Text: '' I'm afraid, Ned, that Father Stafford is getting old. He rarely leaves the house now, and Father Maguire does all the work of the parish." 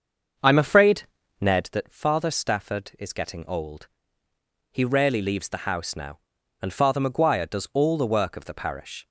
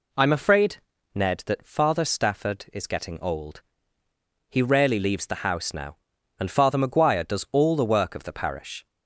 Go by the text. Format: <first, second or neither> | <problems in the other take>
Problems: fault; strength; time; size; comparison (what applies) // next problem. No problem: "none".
second | starts louder than the rest; until 1.7 s; 6.5 dB